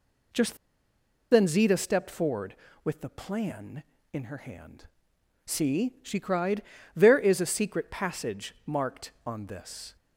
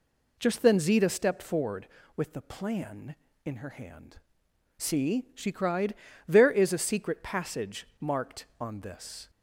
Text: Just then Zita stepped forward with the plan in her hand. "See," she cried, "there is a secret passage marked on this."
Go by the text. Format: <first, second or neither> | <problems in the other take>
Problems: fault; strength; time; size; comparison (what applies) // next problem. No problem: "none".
second | pauses between "Just" and "then"; noticeable; at 0.5 s; 0.76 s long